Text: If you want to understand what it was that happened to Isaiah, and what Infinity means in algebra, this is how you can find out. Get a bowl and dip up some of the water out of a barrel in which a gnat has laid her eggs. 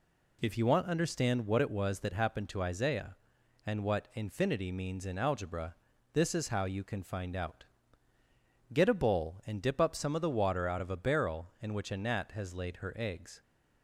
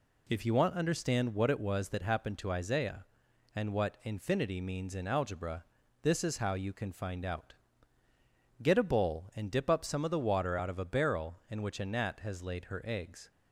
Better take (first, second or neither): neither